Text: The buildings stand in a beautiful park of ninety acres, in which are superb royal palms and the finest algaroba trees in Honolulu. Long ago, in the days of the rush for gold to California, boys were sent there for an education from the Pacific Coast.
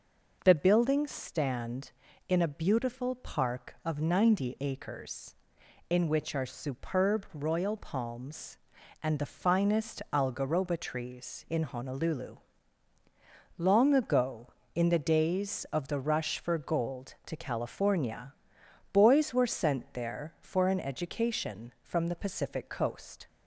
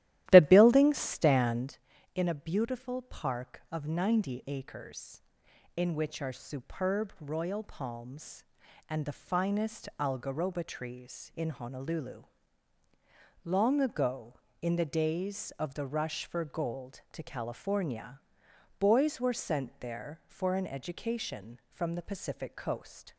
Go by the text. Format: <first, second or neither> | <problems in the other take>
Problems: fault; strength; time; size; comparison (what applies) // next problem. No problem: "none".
first | starts louder than the rest; strong; until 1.7 s; 14 dB